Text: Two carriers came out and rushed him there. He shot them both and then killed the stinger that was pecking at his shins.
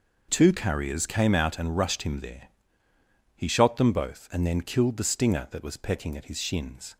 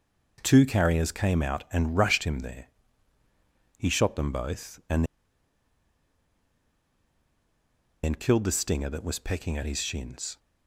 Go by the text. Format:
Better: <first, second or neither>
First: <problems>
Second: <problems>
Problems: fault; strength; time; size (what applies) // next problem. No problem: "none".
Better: first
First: none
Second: pauses between "and" and "then"; strong; at 5.0 s; 2.9 s long